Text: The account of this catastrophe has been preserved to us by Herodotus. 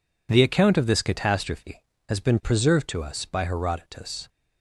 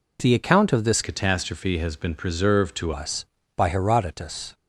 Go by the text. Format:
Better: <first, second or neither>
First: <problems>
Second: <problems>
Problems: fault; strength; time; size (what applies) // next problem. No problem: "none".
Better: first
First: none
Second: changes voice from "catastrophe" to "to"; from 1.0 to 2.9 s; 1.9 s long